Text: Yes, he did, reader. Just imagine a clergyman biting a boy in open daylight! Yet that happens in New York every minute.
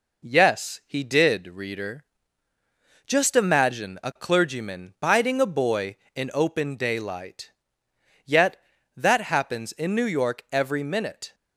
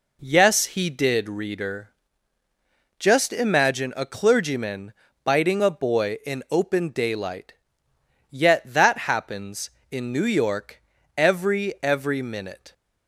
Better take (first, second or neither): first